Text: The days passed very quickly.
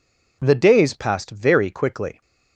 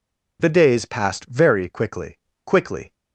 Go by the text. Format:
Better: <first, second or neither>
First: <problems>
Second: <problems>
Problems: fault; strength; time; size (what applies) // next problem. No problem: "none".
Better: first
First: none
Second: says "quickly" twice; at 2.4 s